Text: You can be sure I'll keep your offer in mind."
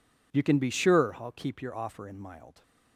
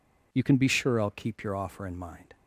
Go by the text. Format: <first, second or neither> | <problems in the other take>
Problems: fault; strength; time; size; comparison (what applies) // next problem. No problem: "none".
second | says "mild" for "mind"; at 2.2 s